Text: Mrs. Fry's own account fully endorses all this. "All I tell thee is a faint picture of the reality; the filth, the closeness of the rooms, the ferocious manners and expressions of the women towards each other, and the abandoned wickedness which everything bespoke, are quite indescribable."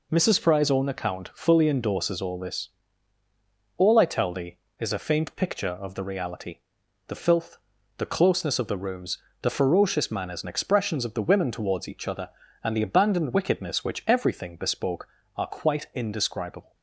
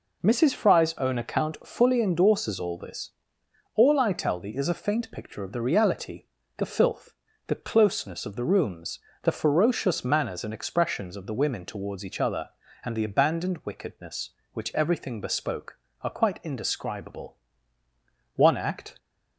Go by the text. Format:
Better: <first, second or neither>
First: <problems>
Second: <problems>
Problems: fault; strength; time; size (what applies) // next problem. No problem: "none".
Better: first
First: none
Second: goes on to say "One act"; noticeable; from 18.3 s on; 0.62 s long